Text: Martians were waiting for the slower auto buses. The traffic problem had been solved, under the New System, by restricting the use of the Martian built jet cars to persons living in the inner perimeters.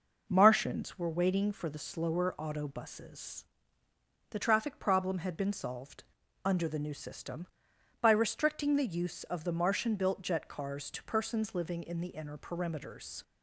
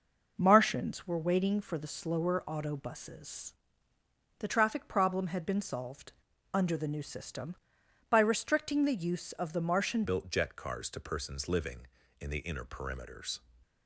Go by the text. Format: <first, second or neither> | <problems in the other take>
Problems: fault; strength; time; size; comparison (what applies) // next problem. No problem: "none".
first | changes voice at "built"; from 10.0 s on; 3.4 s long